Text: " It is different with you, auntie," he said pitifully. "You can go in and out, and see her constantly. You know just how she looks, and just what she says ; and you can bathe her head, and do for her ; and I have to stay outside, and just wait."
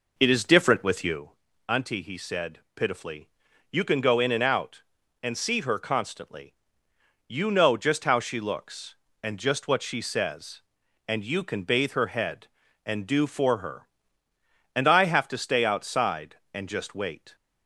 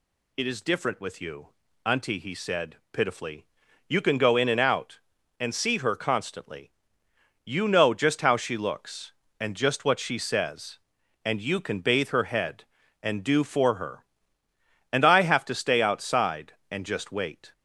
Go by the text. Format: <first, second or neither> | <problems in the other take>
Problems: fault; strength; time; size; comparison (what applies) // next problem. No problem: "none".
second | starts louder than the rest; noticeable; until 1.2 s; 4.5 dB